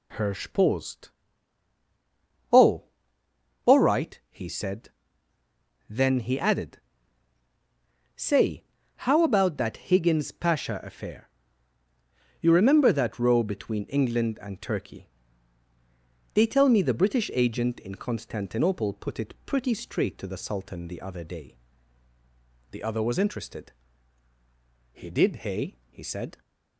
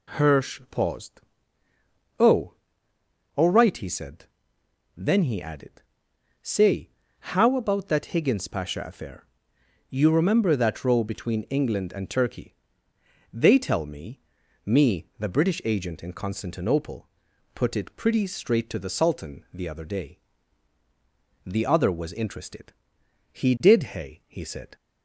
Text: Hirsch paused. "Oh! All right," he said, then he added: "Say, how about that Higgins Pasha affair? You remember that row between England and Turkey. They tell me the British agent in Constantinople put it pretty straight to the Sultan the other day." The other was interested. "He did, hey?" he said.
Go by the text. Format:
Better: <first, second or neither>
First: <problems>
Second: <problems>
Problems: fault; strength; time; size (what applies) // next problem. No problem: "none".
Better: first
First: none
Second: says "me" twice; at 14.6 s // pauses between "Constantinople" and "put"; noticeable; at 17.0 s; 0.46 s long